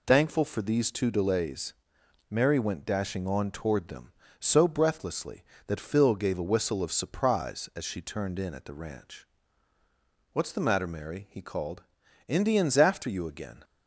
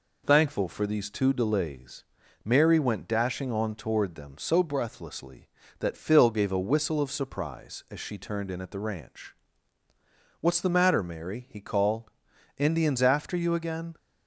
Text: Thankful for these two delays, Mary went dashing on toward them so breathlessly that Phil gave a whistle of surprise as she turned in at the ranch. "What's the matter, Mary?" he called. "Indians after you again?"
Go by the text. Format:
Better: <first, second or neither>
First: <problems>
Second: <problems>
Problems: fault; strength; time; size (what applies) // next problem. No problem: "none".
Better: neither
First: none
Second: none